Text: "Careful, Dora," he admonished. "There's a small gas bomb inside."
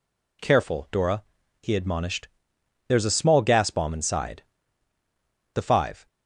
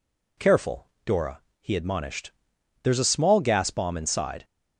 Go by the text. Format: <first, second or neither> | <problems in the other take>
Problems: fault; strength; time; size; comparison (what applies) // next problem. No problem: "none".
second | goes on to say "The five"; from 5.5 s on; 0.52 s long